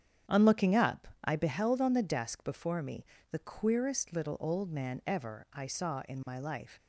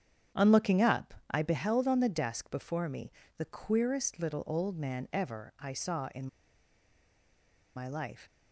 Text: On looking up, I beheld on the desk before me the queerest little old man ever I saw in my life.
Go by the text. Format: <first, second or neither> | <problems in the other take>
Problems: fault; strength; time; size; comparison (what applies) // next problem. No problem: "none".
first | starts louder than the rest; strong; until 1.5 s; 8.5 dB; strong in the first // pauses between "me" and "the"; slight; at 3.1 s; 0.28 s long; slight in the first // pauses between "in" and "my"; strong; at 6.2 s; 1.4 s long